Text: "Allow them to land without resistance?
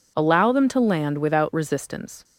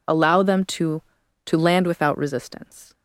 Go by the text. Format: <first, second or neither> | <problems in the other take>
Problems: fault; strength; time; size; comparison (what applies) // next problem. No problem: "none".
first | says "to" twice; at 1.4 s